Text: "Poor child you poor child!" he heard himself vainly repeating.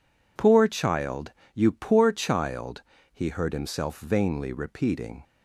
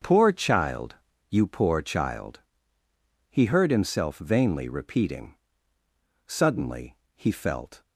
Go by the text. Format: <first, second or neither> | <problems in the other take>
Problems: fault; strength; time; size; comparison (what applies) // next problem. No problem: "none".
first | starts louder than the rest; until 1.3 s; 6.5 dB // pauses between "child" and "you"; slight; at 0.9 s; 0.32 s long; slight in the first // goes on to say "Suddenly he felt"; from 6.2 s on; 1.5 s long